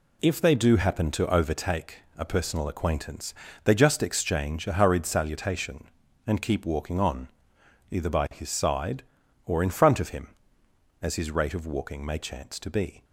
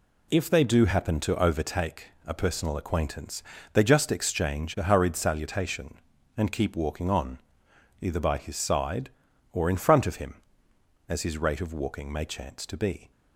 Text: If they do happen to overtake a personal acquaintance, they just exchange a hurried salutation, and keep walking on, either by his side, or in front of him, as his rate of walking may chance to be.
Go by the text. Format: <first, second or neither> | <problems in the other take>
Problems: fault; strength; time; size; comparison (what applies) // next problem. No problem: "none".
neither | pauses between "overtake" and "a"; slight; the same in both